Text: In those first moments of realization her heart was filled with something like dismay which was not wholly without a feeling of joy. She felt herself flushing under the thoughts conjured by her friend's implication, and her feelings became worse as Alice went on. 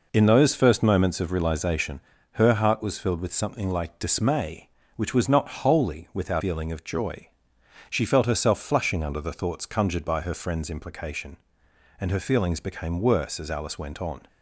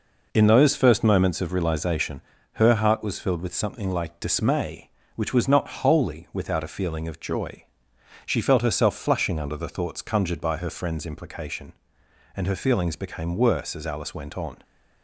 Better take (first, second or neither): second